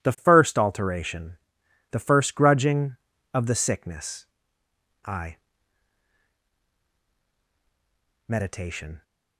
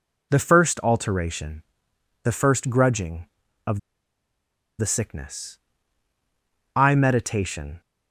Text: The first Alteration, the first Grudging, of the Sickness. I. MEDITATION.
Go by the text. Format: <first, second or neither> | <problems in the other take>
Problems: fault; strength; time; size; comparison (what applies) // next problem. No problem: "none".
first | pauses between "of" and "the"; at 3.7 s; 1.0 s long